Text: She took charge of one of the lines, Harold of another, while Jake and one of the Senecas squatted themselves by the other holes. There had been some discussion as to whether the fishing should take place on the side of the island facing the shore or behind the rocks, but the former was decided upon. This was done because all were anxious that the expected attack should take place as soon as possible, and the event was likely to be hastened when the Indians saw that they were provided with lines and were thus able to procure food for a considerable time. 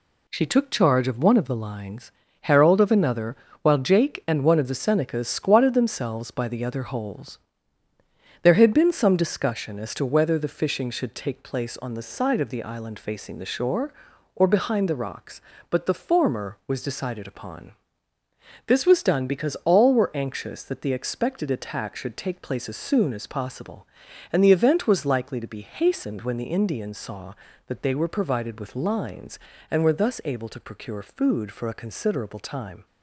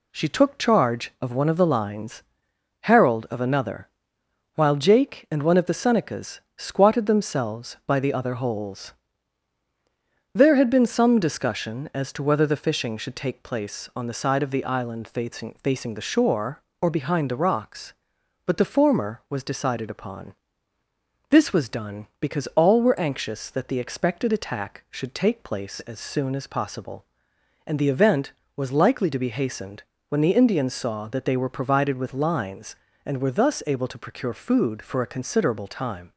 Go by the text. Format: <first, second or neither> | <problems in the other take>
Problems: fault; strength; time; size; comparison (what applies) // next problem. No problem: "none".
first | pauses between "Senecas" and "squatted"; slight; at 6.3 s; 0.16 s long // says "facing" twice; at 15.6 s // pauses between "hastened" and "when"; slight; at 29.8 s; 0.26 s long